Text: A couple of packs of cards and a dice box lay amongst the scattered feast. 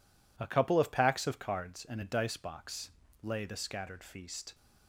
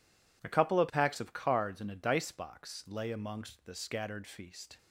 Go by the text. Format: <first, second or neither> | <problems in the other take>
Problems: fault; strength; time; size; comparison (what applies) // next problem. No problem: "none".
second | pauses between "box" and "lay"; slight; at 2.9 s; 0.32 s long // skips "amongst"; at 3.4 s